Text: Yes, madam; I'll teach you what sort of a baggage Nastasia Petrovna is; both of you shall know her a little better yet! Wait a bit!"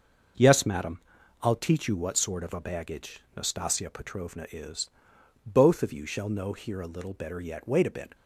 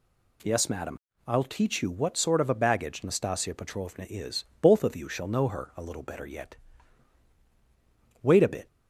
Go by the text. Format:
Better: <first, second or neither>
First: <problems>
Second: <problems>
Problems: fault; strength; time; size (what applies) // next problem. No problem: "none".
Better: second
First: starts louder than the rest; noticeable; until 1.7 s; 6 dB // pauses between "baggage" and "Nastasia"; slight; at 3.2 s; 0.16 s long // says "here" for "her"; at 6.5 s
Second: none